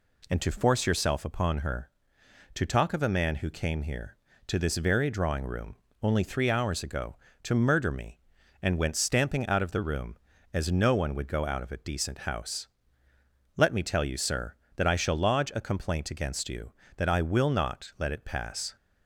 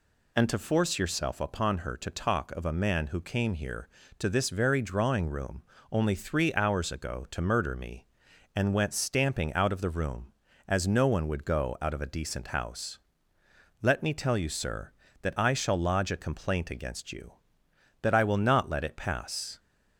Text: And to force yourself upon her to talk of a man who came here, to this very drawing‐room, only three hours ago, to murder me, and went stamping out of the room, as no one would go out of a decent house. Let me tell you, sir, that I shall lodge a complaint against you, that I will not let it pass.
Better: neither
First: none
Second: none

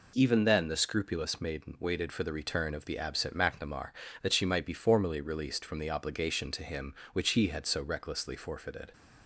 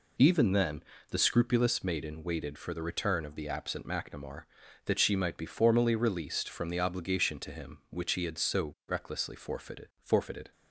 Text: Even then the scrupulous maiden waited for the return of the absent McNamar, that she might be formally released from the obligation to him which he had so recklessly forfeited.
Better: first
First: none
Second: pauses between "then" and "the"; slight; at 0.8 s; 0.28 s long // says "forfeited" twice; at 10.0 s

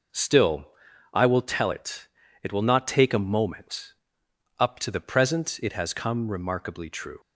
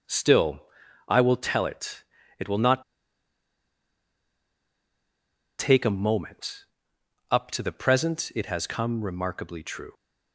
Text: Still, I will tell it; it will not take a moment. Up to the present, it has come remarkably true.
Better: first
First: none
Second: pauses between "not" and "take"; strong; at 2.8 s; 2.7 s long

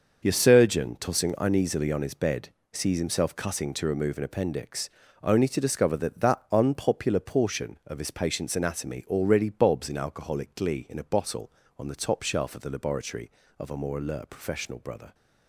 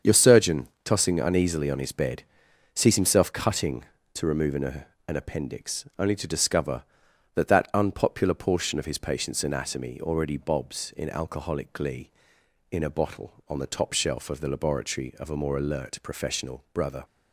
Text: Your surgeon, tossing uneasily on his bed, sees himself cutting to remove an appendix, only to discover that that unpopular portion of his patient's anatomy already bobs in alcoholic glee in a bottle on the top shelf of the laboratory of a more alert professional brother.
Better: first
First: starts louder than the rest; until 1.3 s; 6.5 dB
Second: starts louder than the rest; until 1.2 s; 7 dB // says "an" twice; at 5.0 s

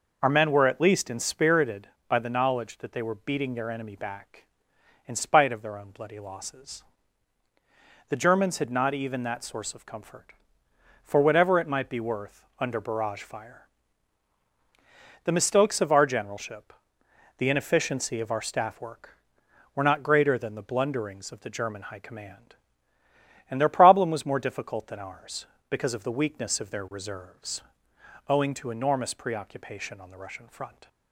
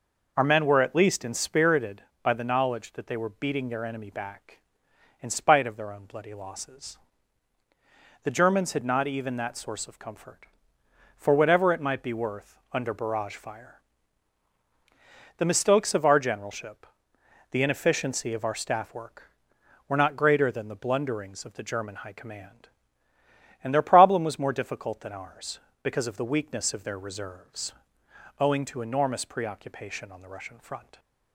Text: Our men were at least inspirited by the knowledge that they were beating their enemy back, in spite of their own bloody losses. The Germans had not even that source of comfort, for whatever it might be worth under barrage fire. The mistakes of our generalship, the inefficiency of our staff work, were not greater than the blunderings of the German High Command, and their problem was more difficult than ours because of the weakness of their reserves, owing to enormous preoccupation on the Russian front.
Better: neither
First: none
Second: none

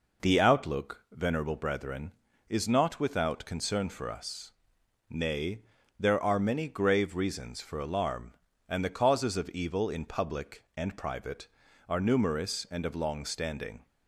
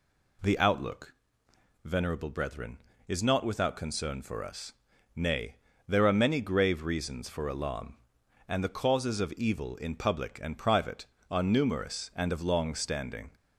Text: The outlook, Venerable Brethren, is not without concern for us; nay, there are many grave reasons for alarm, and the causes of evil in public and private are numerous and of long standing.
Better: neither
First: none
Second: none

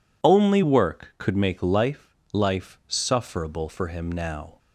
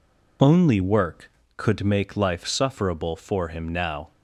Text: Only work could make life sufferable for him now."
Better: second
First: says "life" twice; at 2.3 s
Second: none

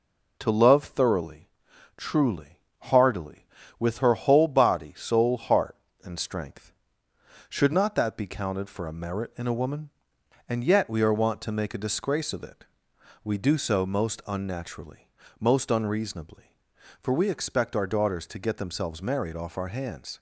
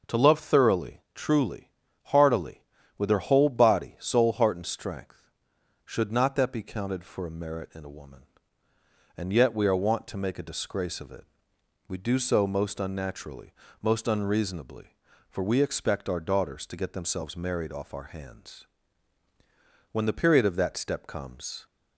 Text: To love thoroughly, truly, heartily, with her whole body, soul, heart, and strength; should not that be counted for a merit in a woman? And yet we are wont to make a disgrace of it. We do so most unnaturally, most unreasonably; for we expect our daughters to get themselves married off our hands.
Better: first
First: none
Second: goes on to say "When the period of that step comes"; strong; from 19.9 s on; 1.7 s long

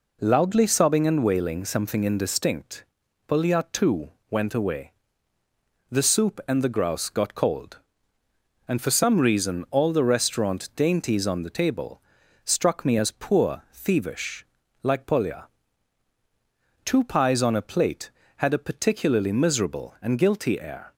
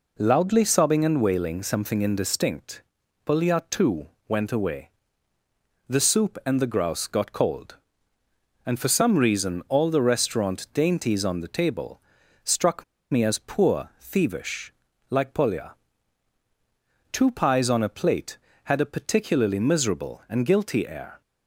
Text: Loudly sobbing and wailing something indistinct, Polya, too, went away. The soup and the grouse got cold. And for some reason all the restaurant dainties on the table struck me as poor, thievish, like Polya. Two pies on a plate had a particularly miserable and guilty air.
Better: first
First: pauses between "table" and "struck"; at 12.0 s; 0.44 s long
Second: pauses between "table" and "struck"; at 12.0 s; 0.44 s long // pauses between "struck" and "me"; slight; at 12.8 s; 0.28 s long

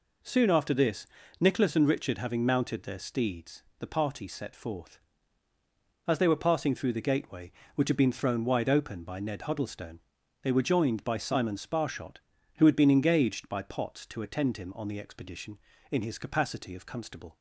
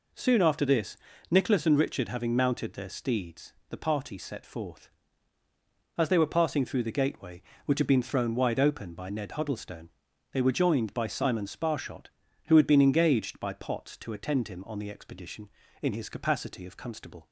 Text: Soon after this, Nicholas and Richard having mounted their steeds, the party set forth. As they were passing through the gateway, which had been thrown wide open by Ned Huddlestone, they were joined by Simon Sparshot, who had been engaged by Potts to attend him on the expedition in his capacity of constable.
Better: neither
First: none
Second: none

